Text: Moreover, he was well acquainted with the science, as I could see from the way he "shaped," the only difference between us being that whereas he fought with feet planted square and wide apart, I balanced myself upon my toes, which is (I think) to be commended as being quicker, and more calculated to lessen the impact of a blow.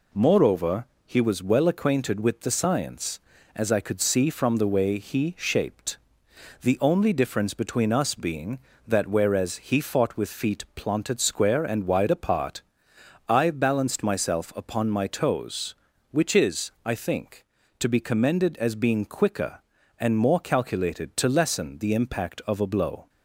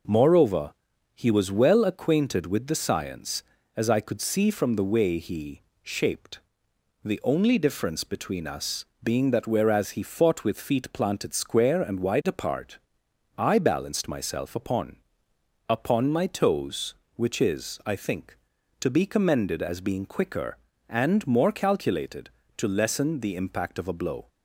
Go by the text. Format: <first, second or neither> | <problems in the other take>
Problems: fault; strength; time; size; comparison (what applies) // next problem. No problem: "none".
first | pauses between "he" and "shaped"; slight; at 5.6 s; 0.20 s long // pauses between "us" and "being"; slight; at 8.8 s; 0.18 s long // says "upon" twice; at 15.6 s